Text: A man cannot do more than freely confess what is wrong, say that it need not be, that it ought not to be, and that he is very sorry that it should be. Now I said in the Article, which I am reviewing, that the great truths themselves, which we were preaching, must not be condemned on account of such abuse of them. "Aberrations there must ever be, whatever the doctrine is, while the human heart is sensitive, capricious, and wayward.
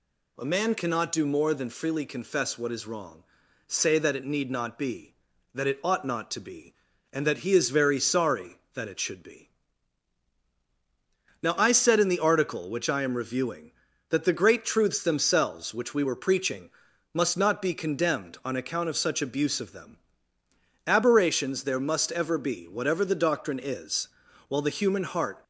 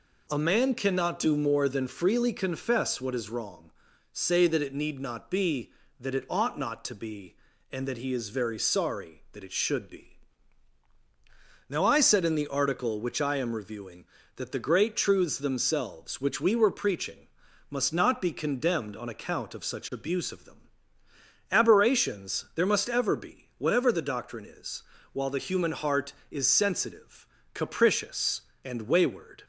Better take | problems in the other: second | stops before "is sensitive capricious and wayward"; at 25.4 s

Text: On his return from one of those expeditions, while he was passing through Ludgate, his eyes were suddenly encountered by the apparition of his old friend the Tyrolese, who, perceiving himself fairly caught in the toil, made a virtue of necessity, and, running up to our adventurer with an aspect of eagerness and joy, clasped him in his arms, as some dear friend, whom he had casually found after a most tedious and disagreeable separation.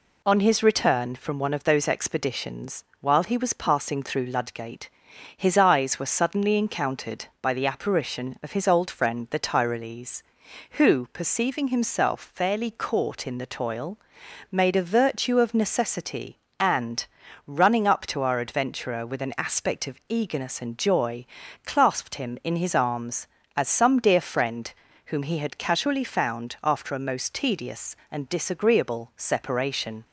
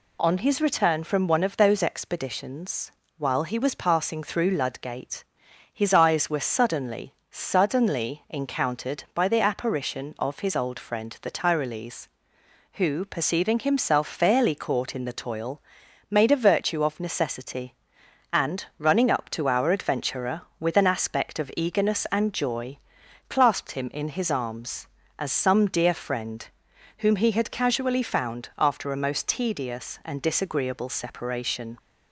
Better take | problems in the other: first | says "suddenly" twice; at 7.3 s

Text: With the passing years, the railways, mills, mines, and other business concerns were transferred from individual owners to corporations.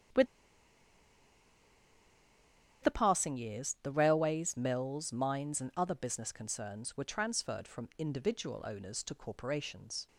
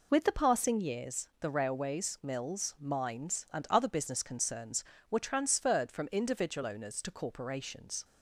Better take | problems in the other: second | starts louder than the rest; strong; until 3.7 s; 8.5 dB // pauses between "With" and "the"; strong; at 0.2 s; 2.5 s long

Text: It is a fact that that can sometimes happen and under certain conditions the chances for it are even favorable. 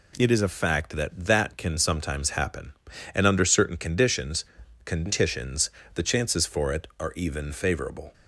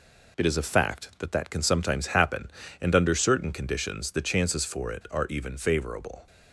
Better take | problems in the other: second | says "conditions" twice; at 4.8 s

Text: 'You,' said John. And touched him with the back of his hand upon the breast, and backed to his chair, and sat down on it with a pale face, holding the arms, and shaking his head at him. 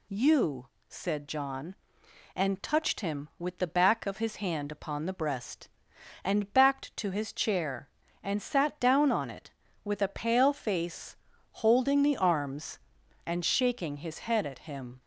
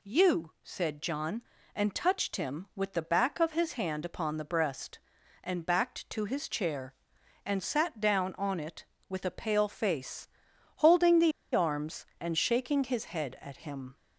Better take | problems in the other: first | pauses between "the" and "arms"; slight; at 11.3 s; 0.23 s long

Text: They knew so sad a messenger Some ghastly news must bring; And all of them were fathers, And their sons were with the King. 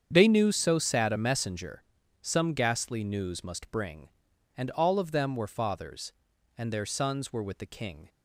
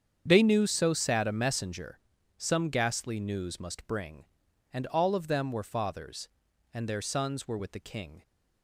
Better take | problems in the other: neither | starts louder than the rest; strong; the same in both // pauses between "messenger" and "Some"; slight; the same in both

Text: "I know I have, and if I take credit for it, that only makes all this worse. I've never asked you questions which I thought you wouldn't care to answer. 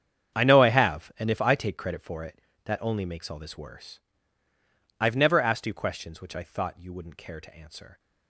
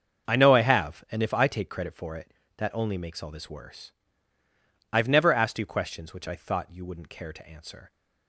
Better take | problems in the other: second | gets quieter; strong; throughout; 16 dB // starts louder than the rest; strong; until 1.4 s; 8 dB; also in the second

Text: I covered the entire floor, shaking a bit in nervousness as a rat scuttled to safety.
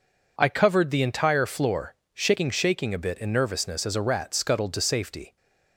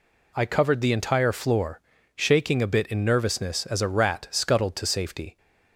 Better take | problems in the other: second | says "shaking" twice; at 2.5 s

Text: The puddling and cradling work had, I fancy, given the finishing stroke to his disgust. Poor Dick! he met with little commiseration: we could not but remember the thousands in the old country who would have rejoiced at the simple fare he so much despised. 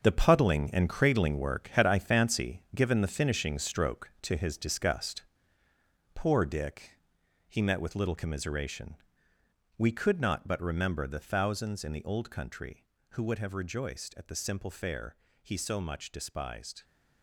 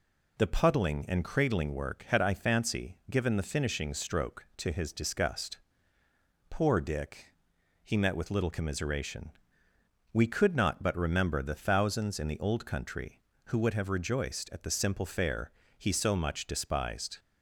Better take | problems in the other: second | gets quieter; strong; throughout; 10.5 dB // pauses between "fare" and "he"; slight; at 15.1 s; 0.26 s long; slight in the second

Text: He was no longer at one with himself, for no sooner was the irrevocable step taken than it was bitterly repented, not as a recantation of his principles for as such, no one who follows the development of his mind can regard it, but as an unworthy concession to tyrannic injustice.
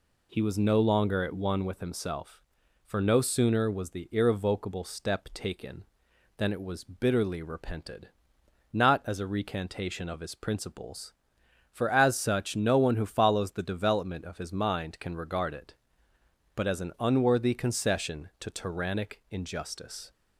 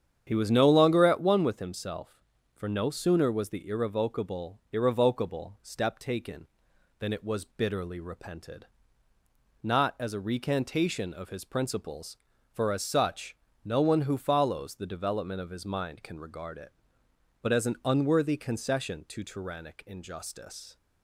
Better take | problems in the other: first | starts louder than the rest; strong; until 1.2 s; 8.5 dB // says "irrevocable" twice; at 4.7 s

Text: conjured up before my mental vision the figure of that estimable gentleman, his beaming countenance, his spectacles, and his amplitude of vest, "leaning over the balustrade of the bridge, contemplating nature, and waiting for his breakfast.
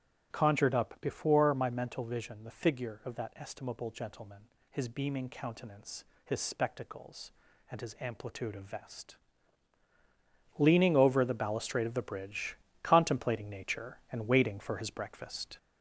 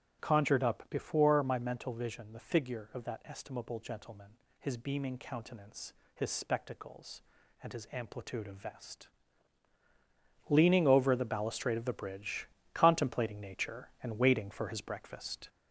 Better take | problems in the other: neither | starts louder than the rest; strong; the same in both

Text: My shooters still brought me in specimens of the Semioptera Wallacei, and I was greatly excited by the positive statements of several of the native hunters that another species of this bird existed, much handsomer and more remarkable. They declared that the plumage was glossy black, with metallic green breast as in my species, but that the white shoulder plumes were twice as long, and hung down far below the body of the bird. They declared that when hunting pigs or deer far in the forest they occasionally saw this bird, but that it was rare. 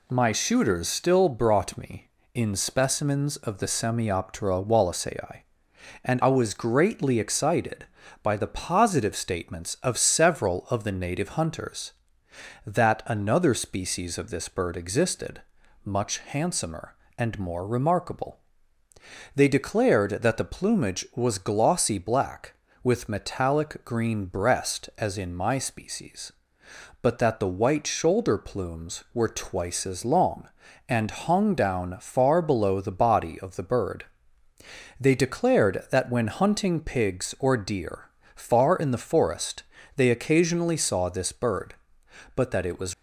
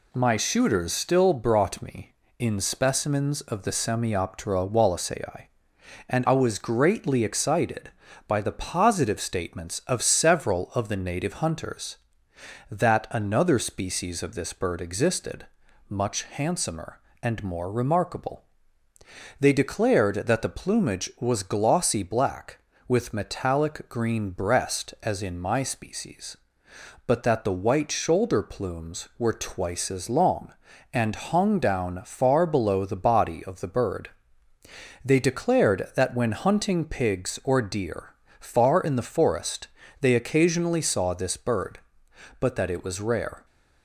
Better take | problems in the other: second | pauses between "deer" and "far"; slight; at 38.1 s; 0.24 s long; slight in the second // pauses between "forest" and "they"; slight; at 39.6 s; 0.32 s long; slight in the second // stops before "rare"; at 42.9 s

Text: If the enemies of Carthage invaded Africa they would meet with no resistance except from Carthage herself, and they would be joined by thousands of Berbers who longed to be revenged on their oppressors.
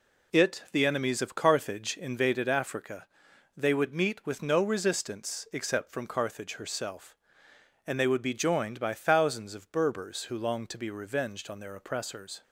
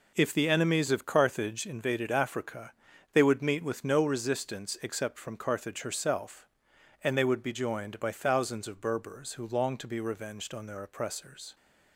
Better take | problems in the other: second | says "It" for "If"; at 0.3 s // pauses between "Africa" and "they"; noticeable; at 3.0 s; 0.50 s long; also in the second

